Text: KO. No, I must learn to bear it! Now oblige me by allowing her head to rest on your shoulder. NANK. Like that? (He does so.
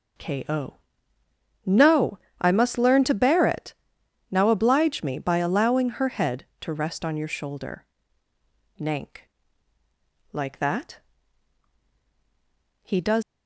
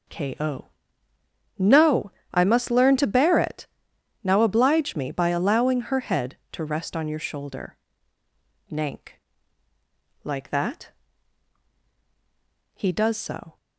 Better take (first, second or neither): second